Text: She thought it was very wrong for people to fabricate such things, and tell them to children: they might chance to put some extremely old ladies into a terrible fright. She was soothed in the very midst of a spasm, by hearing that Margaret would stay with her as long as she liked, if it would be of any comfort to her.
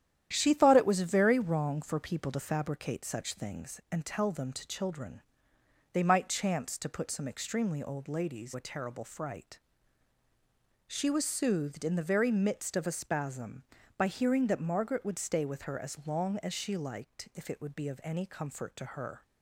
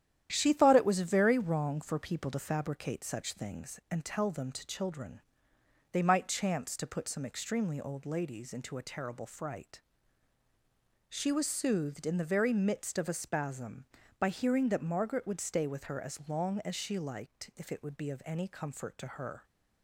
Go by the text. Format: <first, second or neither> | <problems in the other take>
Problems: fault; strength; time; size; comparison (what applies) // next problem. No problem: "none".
second | starts louder than the rest; strong; until 1.3 s; 10.5 dB; strong in the second // skips "into"; at 8.5 s